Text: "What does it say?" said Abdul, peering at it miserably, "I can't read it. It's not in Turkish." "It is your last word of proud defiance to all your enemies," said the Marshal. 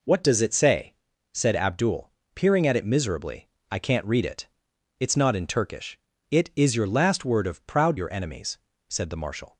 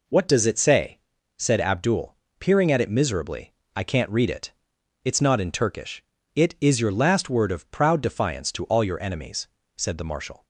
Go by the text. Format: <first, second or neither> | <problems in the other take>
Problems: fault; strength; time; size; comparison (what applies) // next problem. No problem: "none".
second | skips "defiance to all"; at 7.9 s